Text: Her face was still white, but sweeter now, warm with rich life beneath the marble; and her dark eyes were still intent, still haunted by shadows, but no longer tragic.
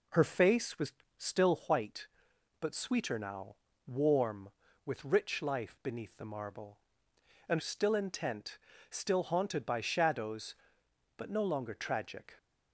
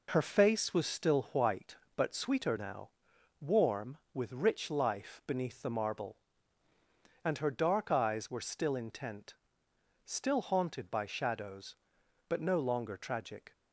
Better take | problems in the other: second | pauses between "was" and "still"; slight; at 0.9 s; 0.26 s long // skips "her dark eyes were"; at 7.5 s

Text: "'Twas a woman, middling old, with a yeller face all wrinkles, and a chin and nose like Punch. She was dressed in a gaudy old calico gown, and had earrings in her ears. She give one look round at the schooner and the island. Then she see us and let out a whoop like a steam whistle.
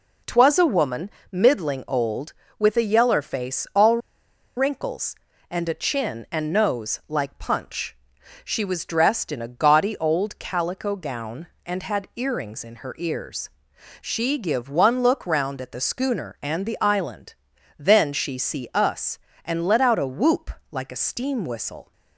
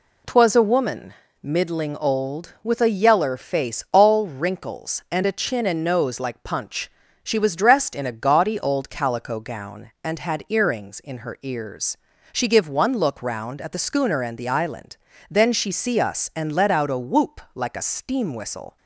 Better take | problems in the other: second | pauses between "all" and "wrinkles"; noticeable; at 3.9 s; 0.59 s long // pauses between "whoop" and "like"; slight; at 20.4 s; 0.20 s long

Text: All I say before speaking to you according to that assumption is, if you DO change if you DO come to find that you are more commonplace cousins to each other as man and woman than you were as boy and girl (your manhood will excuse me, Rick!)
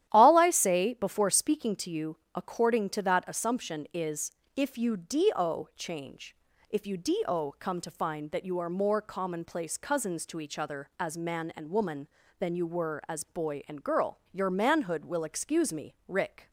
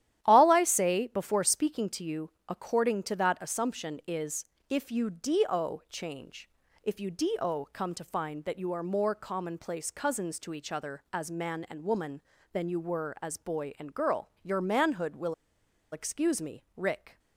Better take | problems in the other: first | starts louder than the rest; strong; until 1.2 s; 12 dB; strong in the first // pauses between "you" and "according"; slight; at 2.2 s; 0.18 s long; slight in the first // pauses between "change" and "if"; slight; at 6.4 s; 0.36 s long; slight in the first // pauses between "will" and "excuse"; noticeable; at 15.3 s; 0.59 s long

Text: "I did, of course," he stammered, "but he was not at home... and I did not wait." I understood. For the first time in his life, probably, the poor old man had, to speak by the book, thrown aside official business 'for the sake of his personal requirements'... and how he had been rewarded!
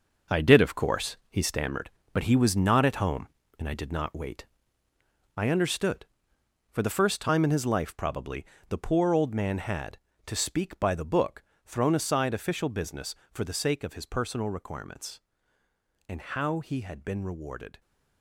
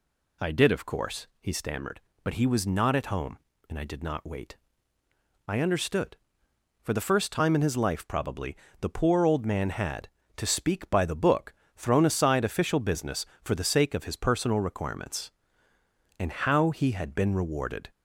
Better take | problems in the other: second | gets quieter; strong; throughout; 9 dB

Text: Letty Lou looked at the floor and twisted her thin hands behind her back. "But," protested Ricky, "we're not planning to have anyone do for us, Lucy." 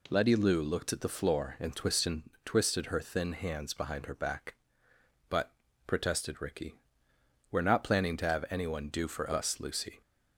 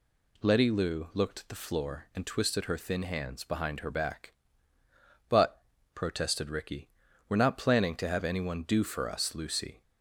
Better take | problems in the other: second | says "twisted" twice; at 2.4 s

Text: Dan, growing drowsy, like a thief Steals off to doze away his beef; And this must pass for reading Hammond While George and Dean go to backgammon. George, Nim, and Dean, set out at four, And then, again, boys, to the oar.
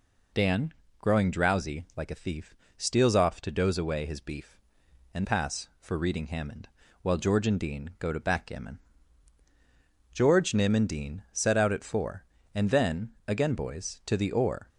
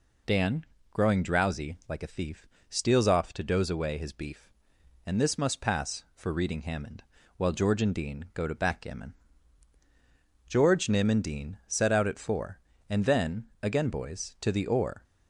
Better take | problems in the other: second | pauses between "thief" and "Steals"; slight; at 2.5 s; 0.24 s long; slight in the second // skips "this must"; at 5.2 s // pauses between "Hammond" and "While"; slight; at 6.6 s; 0.34 s long; slight in the second

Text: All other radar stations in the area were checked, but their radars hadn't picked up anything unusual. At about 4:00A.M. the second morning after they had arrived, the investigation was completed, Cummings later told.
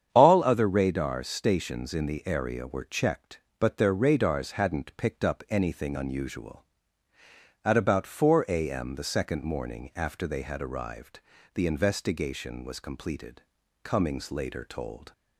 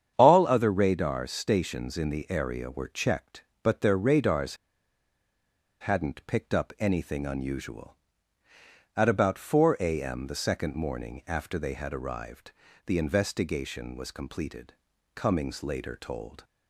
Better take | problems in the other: first | starts louder than the rest; strong; until 1.1 s; 8.5 dB; strong in the first // pauses between "radars" and "hadn't"; strong; at 4.5 s; 1.2 s long

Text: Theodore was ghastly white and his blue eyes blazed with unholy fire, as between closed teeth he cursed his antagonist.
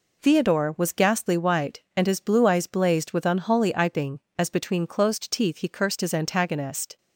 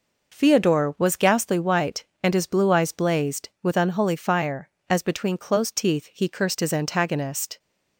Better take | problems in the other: second | says "iping" for "fire"; at 3.7 s

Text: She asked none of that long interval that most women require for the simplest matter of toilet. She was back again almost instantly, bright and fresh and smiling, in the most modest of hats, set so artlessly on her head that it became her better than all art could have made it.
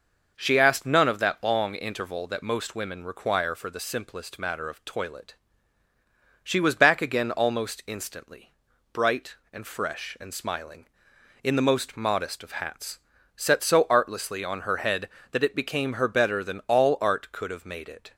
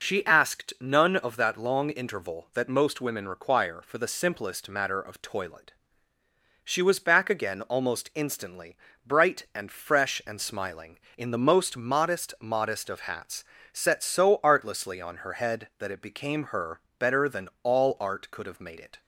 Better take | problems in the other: first | says "modest" twice; at 12.4 s // pauses between "her" and "better"; slight; at 16.8 s; 0.18 s long

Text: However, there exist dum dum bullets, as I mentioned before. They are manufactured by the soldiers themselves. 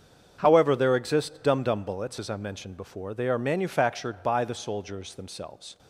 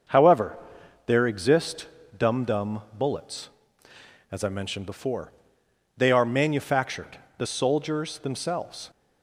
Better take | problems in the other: first | starts louder than the rest; until 1.5 s; 6.5 dB; strong in the first // pauses between "exist" and "dum"; slight; at 1.8 s; 0.32 s long // pauses between "dum" and "bullets"; slight; at 2.8 s; 0.16 s long // skips "by"; at 7.2 s

